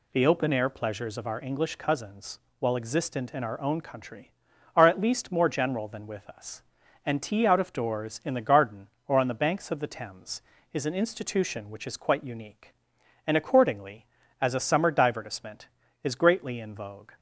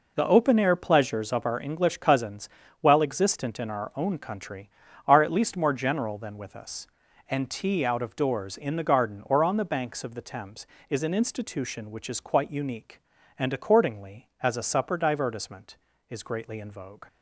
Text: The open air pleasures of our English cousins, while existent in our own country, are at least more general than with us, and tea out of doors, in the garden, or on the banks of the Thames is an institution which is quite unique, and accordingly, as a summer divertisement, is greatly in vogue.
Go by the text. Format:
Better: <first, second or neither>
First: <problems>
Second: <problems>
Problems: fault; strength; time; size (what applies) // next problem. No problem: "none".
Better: first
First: none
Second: says "supper" for "summer"; at 14.6 s